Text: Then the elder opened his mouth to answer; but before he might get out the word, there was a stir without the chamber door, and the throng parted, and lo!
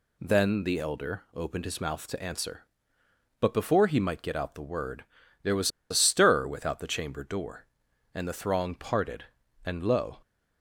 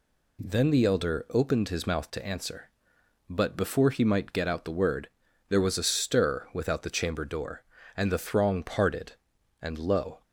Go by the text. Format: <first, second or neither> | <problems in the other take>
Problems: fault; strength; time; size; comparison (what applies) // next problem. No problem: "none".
second | pauses between "was" and "a"; slight; at 5.6 s; 0.20 s long